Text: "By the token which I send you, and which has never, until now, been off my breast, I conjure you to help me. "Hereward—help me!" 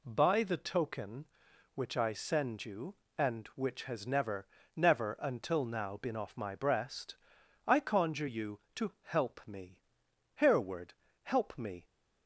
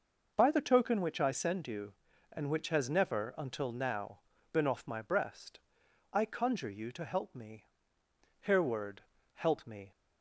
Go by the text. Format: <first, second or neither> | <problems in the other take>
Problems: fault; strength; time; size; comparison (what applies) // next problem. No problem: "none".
second | says "never" twice; at 4.7 s